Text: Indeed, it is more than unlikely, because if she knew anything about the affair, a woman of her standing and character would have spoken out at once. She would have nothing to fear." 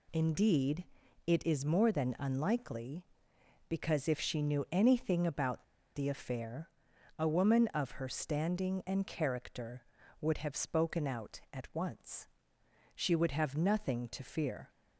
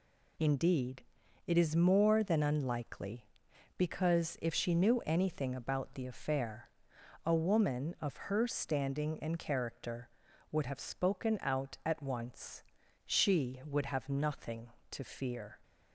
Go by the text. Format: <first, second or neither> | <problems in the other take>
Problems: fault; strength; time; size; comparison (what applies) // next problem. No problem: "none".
second | pauses between "about" and "the"; slight; at 5.6 s; 0.31 s long